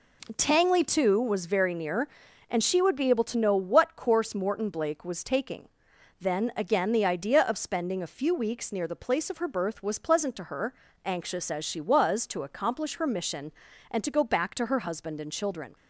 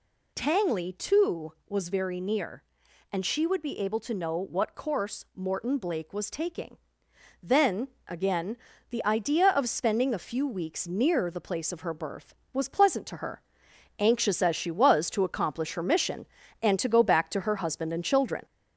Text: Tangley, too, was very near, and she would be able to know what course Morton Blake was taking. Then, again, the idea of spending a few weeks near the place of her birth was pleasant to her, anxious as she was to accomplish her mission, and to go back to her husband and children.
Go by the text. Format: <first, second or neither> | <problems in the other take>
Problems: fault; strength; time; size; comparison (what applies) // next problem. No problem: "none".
first | gets louder; slight; throughout; 2.5 dB